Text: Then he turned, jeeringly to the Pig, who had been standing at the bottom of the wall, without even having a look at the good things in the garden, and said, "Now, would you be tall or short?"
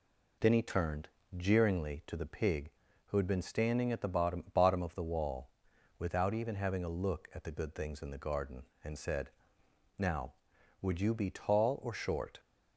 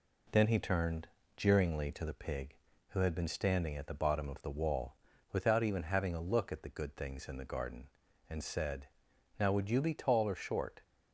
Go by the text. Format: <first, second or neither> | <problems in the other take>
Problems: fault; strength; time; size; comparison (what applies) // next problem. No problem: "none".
second | says "bottom" twice; at 4.5 s